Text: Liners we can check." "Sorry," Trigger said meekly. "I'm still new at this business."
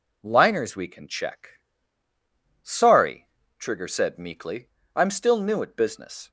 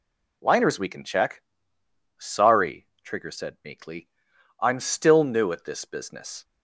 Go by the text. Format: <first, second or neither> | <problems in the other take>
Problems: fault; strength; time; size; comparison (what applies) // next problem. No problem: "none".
second | skips "this"; at 5.7 s